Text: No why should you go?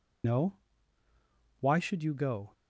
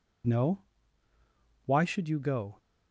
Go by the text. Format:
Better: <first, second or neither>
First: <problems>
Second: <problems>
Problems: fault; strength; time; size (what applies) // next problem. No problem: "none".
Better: second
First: loses the start of "No"; at 0.2 s; 55 ms // pauses between "No" and "why"; at 0.5 s; 1.0 s long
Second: pauses between "No" and "why"; at 0.6 s; 1.0 s long